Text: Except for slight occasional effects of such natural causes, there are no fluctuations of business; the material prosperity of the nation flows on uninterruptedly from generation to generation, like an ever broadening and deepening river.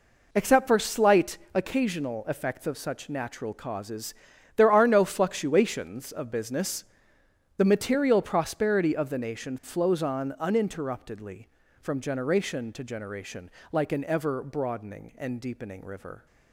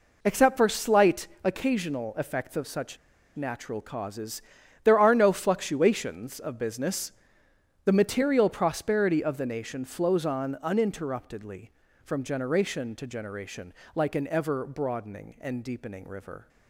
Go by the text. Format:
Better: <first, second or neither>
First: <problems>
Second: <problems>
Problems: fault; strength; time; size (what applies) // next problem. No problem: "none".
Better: first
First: pauses between "slight" and "occasional"; slight; at 1.3 s; 0.16 s long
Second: pauses between "slight" and "occasional"; slight; at 1.2 s; 0.16 s long // pauses between "such" and "natural"; at 2.9 s; 0.39 s long